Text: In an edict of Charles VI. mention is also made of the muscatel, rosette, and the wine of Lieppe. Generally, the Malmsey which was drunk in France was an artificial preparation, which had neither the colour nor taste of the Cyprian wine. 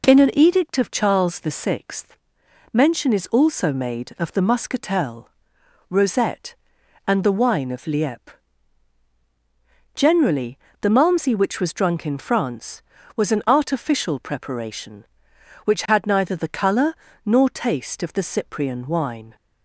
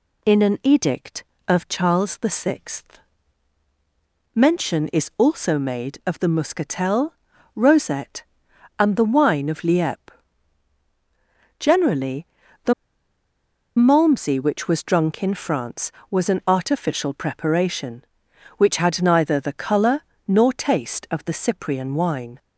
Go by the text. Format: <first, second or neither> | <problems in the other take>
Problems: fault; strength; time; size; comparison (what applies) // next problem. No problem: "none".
first | pauses between "the" and "Malmsey"; at 12.7 s; 1.0 s long // pauses between "colour" and "nor"; slight; at 20.0 s; 0.26 s long; slight in the first